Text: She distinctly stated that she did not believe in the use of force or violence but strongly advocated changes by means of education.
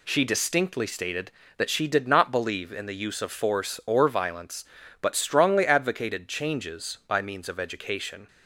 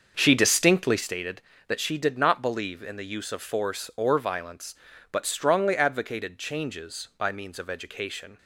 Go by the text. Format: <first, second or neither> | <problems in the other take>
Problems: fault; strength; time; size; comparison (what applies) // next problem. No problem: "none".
first | starts louder than the rest; until 1.2 s; 6.5 dB